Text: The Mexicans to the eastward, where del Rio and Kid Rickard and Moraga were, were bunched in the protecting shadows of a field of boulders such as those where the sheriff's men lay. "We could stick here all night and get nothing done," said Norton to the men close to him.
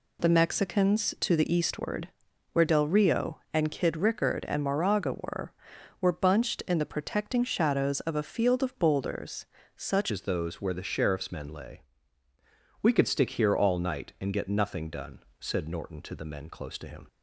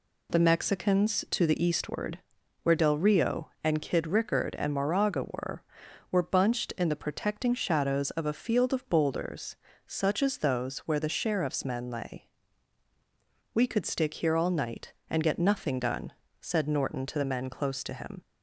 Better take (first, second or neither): second